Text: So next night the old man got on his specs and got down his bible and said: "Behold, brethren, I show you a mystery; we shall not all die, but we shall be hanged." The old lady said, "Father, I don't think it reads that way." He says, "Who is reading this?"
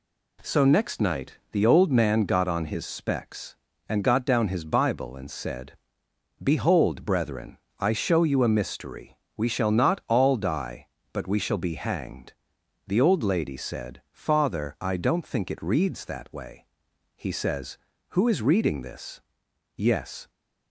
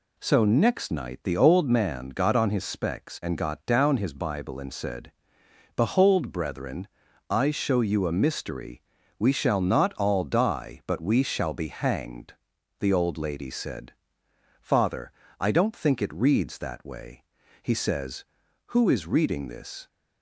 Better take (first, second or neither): second